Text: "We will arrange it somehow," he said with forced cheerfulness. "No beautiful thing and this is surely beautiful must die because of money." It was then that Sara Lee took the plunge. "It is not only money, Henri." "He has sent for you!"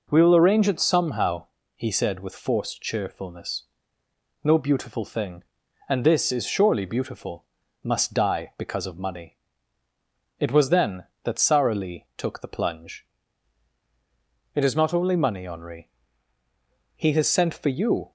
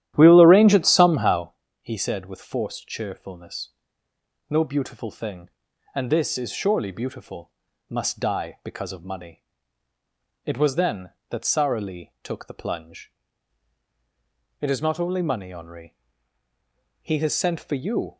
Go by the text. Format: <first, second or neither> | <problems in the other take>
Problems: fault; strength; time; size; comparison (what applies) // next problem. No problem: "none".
first | starts louder than the rest; strong; until 1.5 s; 12 dB // pauses between "beautiful" and "must"; at 7.4 s; 0.40 s long; also in the first